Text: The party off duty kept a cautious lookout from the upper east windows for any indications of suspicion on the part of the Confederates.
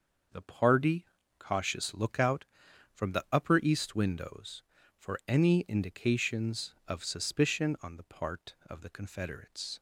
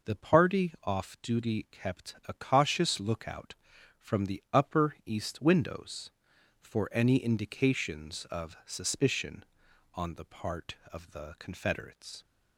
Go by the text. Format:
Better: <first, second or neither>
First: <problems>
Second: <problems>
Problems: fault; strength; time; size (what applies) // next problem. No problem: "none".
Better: second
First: starts louder than the rest; noticeable; until 1.6 s; 6 dB // skips "off duty kept a"; at 1.2 s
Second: none